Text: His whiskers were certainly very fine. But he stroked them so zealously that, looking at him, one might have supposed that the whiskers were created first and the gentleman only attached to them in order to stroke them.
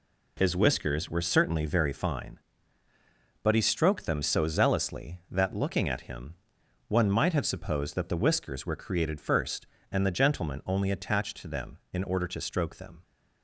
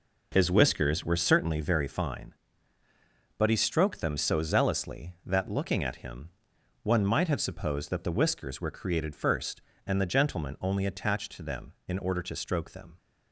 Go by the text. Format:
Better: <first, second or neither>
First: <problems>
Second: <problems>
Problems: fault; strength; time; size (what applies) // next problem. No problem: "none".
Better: first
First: none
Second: starts louder than the rest; noticeable; until 1.5 s; 4 dB